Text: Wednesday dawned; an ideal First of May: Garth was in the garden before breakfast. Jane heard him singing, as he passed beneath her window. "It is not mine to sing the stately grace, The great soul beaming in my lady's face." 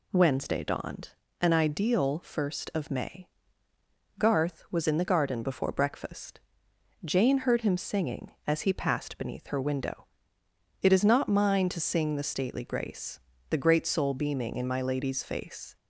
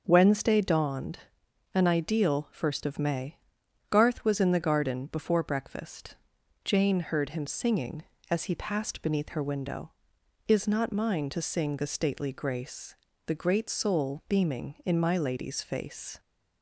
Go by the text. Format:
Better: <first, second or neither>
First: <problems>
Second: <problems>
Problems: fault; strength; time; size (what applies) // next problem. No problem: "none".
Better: first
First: none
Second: starts louder than the rest; noticeable; until 1.0 s; 6 dB // skips "It"; at 10.1 s